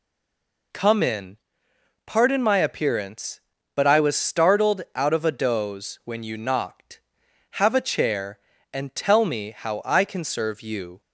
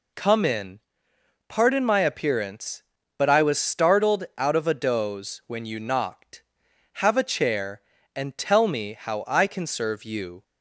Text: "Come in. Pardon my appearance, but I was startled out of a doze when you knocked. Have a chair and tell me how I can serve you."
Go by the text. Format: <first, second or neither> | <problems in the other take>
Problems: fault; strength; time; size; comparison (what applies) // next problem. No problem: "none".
second | stays silent before the first word; slight; until 0.7 s; 0.7 s long